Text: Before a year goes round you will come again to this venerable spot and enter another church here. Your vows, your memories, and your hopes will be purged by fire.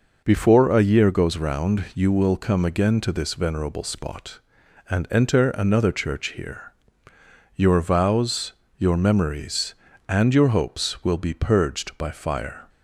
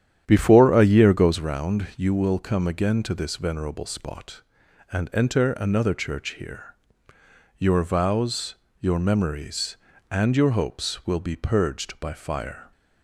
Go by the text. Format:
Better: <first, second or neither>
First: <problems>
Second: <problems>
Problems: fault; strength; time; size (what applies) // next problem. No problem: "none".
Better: first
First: none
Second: starts louder than the rest; strong; until 1.4 s; 10 dB